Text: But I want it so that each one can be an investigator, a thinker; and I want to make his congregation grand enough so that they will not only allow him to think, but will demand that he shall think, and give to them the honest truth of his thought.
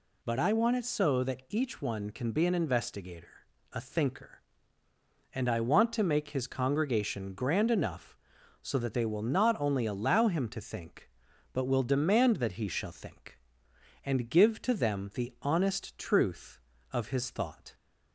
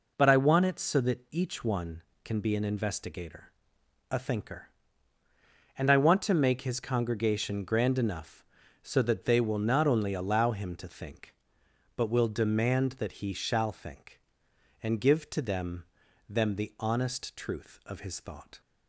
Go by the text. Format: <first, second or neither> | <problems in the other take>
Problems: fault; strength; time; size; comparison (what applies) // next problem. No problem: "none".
first | says "them" twice; at 16.2 s